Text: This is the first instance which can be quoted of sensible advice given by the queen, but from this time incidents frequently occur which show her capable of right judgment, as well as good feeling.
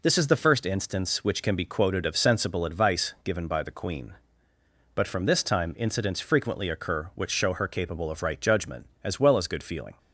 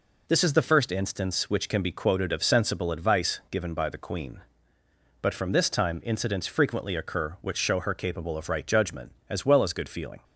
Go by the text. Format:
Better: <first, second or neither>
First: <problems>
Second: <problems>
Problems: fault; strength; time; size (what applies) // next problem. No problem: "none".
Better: neither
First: none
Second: none